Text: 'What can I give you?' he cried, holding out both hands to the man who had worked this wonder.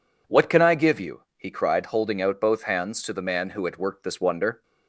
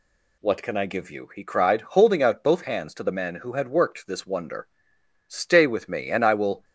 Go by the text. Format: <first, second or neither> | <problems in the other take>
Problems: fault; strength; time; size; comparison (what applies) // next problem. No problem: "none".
first | goes on to say "Stay with me and I will"; from 5.2 s on; 1.3 s long